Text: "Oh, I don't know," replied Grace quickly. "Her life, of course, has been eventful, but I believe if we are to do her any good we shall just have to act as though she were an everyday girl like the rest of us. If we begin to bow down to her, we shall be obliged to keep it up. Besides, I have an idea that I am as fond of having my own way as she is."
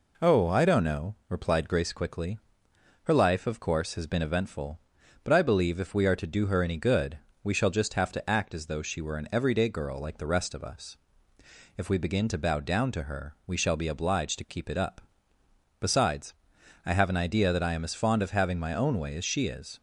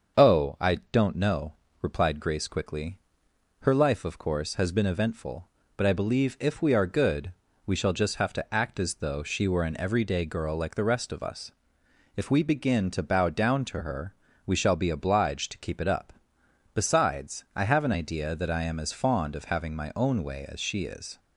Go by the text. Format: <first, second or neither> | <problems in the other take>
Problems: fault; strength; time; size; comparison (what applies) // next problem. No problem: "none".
first | starts louder than the rest; until 1.3 s; 7 dB // pauses between "I" and "don't"; slight; at 0.7 s; 0.16 s long // skips "to do her any"; at 6.8 s // pauses between "good" and "we"; slight; at 7.3 s; 0.32 s long; slight in the first